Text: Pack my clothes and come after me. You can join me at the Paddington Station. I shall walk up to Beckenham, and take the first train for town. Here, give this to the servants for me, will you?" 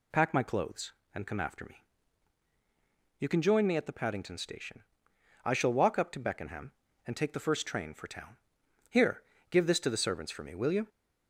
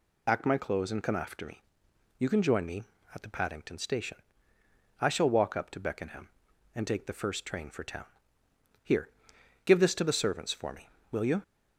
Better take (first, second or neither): first